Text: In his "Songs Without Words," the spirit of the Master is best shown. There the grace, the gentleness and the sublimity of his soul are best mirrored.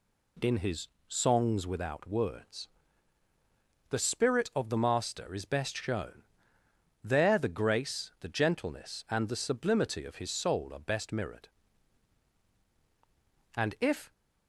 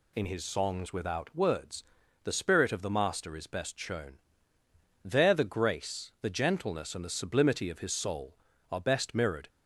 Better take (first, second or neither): second